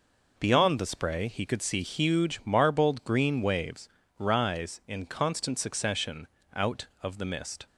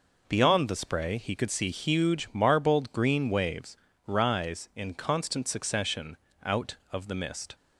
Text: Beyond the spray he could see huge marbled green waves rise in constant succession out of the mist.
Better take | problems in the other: neither | pauses between "waves" and "rise"; slight; the same in both // pauses between "succession" and "out"; slight; the same in both

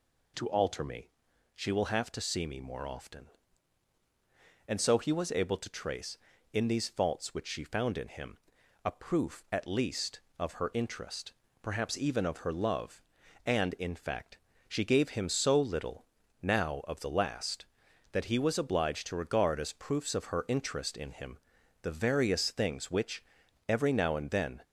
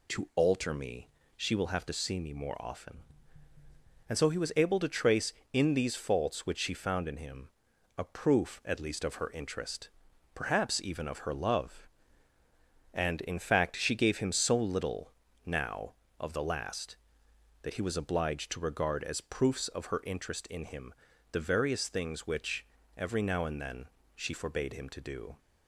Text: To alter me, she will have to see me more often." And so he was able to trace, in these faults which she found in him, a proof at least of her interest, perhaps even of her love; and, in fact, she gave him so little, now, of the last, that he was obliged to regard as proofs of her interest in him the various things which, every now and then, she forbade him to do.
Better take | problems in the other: second | pauses between "him" and "the"; at 21.3 s; 0.44 s long; also in the second // stops before "she forbade him to do"; at 24.6 s

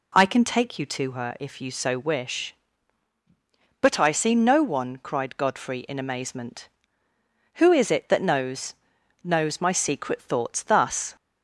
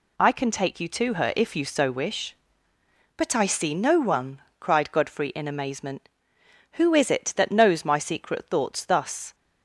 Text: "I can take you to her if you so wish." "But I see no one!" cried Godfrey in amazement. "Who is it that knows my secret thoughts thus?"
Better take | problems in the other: second | says "knows" twice; at 9.2 s

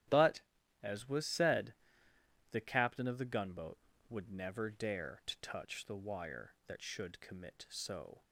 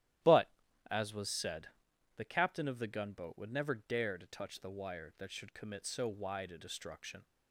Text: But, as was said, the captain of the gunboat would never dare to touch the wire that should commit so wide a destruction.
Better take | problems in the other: second | starts louder than the rest; strong; until 1.4 s; 12 dB; strong in the second // stops before "wide a destruction"; at 8.2 s

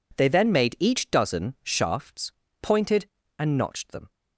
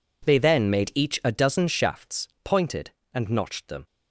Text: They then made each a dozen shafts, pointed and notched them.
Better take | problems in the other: second | skips "a"; at 1.1 s

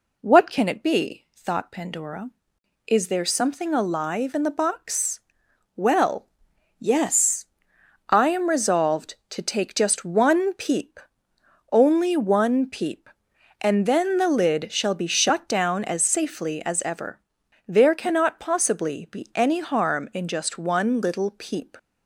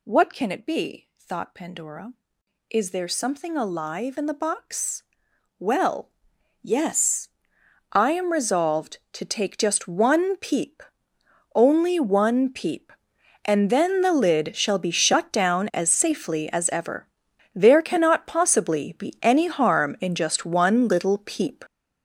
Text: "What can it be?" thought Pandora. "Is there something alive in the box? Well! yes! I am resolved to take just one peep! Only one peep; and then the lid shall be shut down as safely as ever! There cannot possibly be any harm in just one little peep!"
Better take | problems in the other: first | gets louder; strong; throughout; 9 dB

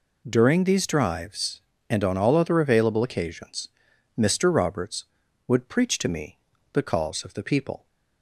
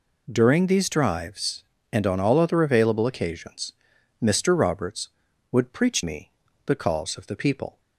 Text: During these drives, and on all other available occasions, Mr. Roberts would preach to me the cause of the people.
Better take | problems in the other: first | skips "to"; at 6.0 s // pauses between "me" and "the"; slight; at 6.2 s; 0.36 s long; slight in the first

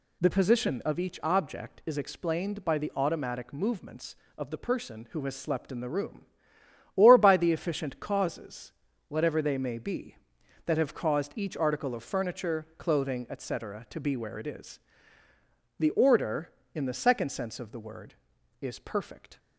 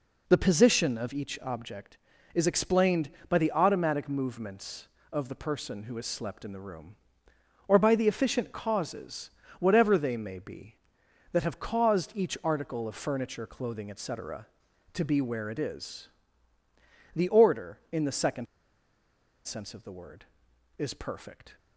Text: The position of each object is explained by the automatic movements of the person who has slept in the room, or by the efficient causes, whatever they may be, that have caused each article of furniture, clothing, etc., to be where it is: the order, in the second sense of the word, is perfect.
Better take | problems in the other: first | pauses between "second" and "sense"; at 18.4 s; 0.99 s long

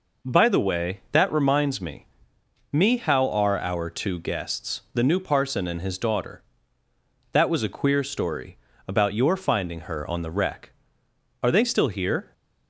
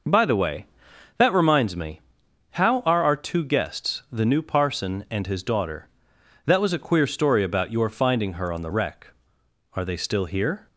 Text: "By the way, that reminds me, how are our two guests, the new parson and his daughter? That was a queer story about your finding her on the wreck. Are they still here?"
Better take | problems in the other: second | says "me" twice; at 2.7 s // pauses between "story" and "about"; slight; at 8.5 s; 0.28 s long

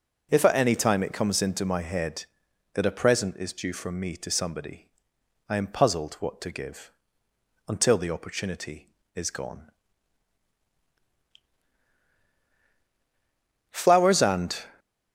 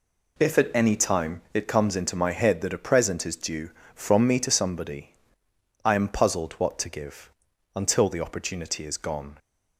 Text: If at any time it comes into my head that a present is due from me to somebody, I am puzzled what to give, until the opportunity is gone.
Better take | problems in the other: second | goes on to say "Flowers and"; noticeable; from 13.7 s on; 1.0 s long

